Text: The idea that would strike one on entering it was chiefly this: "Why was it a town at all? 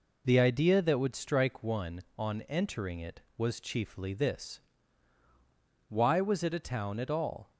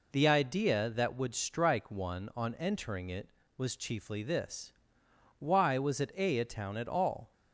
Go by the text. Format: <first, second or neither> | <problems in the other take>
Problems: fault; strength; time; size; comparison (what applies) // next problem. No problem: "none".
first | says "a" twice; at 6.3 s